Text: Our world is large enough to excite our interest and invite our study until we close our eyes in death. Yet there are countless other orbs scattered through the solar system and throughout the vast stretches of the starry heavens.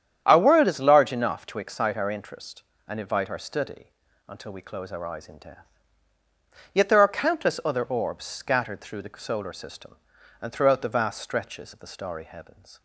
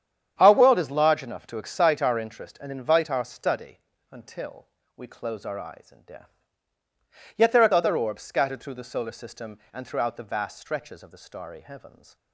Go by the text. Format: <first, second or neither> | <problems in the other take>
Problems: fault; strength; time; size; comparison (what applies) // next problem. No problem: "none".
first | starts louder than the rest; strong; until 1.3 s; 9 dB; strong in the first // pauses between "study" and "until"; slight; at 3.7 s; 0.32 s long; also in the first // pauses between "until" and "we"; slight; at 4.6 s; 0.28 s long // skips "countless"; at 7.7 s